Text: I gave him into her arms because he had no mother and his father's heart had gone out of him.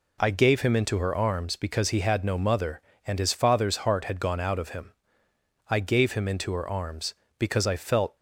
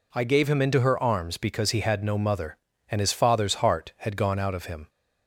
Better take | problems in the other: second | goes on to say "I gave him into her arms because I felt"; strong; from 5.6 s on; 2.4 s long

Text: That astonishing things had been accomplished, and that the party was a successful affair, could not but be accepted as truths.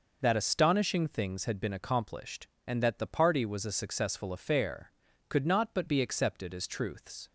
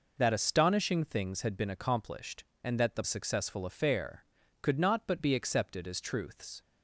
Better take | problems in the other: first | skips "party was a"; at 3.0 s

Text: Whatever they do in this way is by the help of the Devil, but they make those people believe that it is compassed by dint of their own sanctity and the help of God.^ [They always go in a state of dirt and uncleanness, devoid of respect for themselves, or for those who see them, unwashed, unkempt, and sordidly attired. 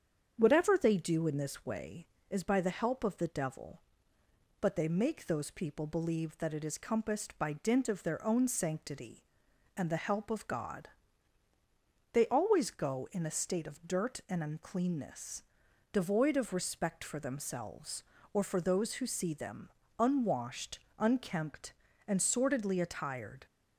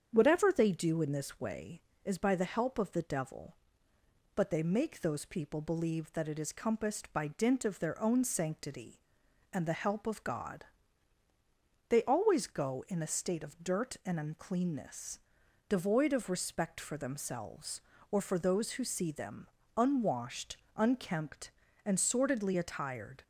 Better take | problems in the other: neither | starts louder than the rest; strong; the same in both

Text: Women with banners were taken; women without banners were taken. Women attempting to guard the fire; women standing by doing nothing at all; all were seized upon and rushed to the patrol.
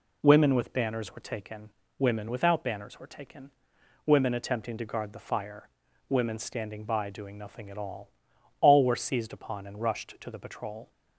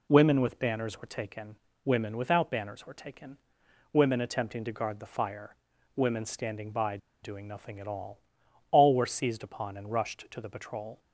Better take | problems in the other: first | pauses between "by" and "doing"; slight; at 6.9 s; 0.25 s long

